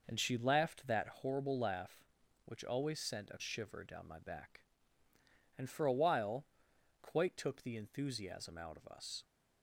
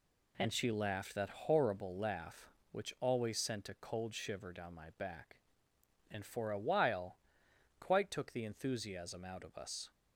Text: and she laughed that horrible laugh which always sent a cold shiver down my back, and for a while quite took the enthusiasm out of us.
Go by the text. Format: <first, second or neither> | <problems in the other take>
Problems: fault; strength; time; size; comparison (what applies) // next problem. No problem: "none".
second | skips "cold"; at 3.4 s // pauses between "while" and "quite"; noticeable; at 6.4 s; 0.58 s long; noticeable in the second